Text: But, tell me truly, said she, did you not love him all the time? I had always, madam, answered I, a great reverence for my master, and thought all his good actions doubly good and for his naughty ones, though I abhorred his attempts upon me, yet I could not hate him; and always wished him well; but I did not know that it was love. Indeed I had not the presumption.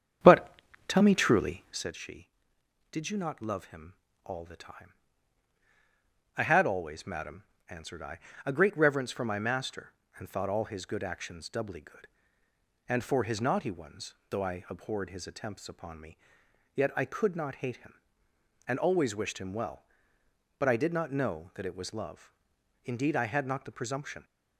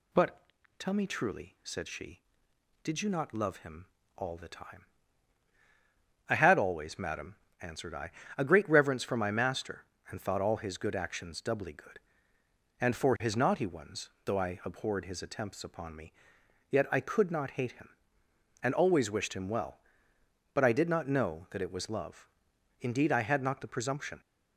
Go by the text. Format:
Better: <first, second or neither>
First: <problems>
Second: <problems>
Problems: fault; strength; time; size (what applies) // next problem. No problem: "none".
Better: second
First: starts louder than the rest; strong; until 1.9 s; 8.5 dB // pauses between "him" and "all"; slight; at 3.9 s; 0.30 s long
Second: pauses between "him" and "all"; slight; at 3.8 s; 0.30 s long